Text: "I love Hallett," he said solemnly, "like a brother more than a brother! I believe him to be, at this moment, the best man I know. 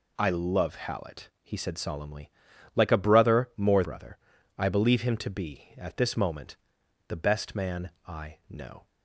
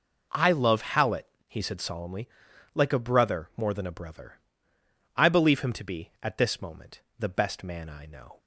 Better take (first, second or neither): second